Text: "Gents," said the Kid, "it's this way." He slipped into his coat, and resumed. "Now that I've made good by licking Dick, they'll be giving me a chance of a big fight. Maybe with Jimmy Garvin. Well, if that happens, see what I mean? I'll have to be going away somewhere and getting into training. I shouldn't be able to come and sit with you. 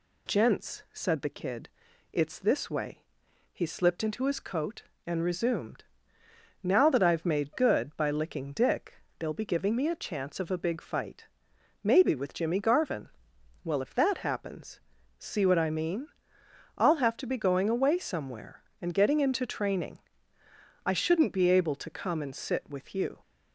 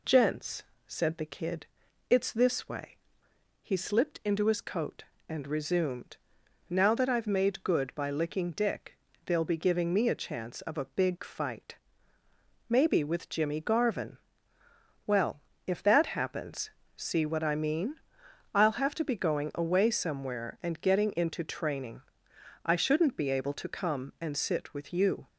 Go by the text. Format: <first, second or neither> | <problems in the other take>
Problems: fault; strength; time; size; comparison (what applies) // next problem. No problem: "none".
neither | none